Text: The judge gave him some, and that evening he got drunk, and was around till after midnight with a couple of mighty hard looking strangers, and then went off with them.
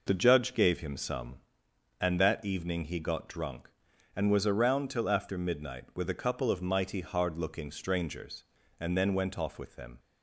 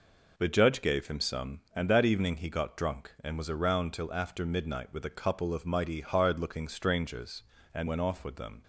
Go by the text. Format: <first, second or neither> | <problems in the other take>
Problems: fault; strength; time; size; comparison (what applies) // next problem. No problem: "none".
first | skips "then"; at 7.8 s